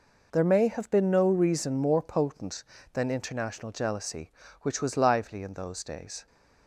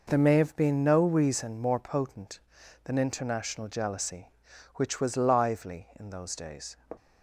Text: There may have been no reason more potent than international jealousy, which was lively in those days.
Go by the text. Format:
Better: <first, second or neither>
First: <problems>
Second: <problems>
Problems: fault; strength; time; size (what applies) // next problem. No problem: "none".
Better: neither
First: none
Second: none